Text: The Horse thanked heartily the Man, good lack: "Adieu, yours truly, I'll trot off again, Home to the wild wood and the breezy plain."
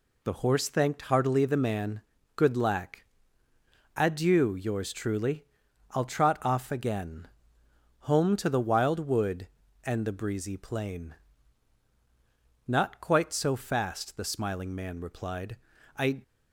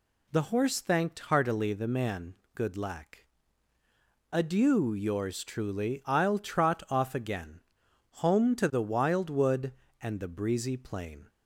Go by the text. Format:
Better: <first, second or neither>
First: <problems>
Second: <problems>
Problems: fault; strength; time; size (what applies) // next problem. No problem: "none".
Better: second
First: goes on to say "Not quite so fast the smiling Man replied I"; strong; from 12.6 s on; 3.5 s long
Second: none